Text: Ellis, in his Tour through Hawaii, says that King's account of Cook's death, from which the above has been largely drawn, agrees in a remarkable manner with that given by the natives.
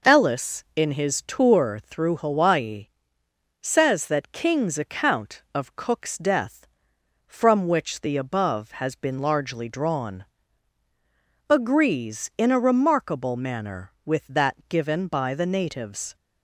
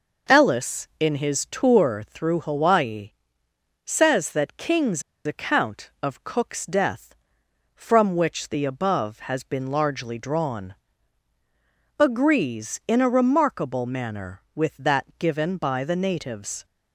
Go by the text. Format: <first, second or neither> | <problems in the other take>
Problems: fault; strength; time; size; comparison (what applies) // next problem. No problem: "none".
first | pauses between "King's" and "account"; slight; at 5.0 s; 0.23 s long